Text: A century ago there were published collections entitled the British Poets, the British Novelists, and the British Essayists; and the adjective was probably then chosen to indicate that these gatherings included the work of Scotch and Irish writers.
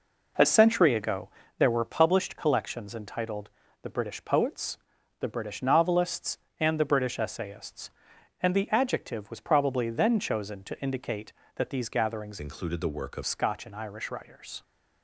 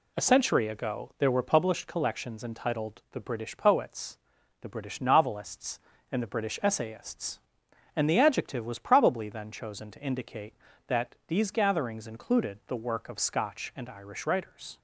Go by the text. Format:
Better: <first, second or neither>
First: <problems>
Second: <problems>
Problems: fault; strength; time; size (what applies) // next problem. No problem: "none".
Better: second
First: pauses between "ago" and "there"; slight; at 1.2 s; 0.28 s long // pauses between "entitled" and "the"; slight; at 3.4 s; 0.32 s long // changes voice from "included" to "of"; from 12.4 to 13.2 s; 0.8 s long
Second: none